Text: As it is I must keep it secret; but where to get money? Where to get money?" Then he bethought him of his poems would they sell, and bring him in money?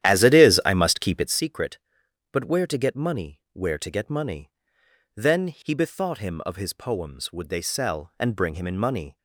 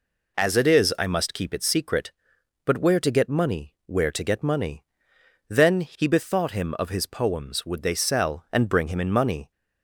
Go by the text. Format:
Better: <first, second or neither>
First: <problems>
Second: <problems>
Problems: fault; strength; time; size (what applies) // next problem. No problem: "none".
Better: second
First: starts louder than the rest; strong; until 1.4 s; 11.5 dB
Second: none